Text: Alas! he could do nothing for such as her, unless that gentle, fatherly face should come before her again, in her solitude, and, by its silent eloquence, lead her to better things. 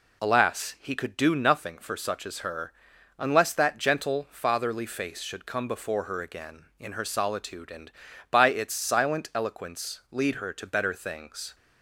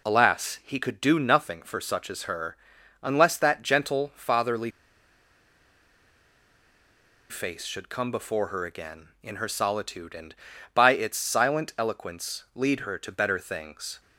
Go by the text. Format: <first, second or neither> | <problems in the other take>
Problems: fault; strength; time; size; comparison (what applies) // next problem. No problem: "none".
first | pauses between "fatherly" and "face"; strong; at 4.7 s; 2.5 s long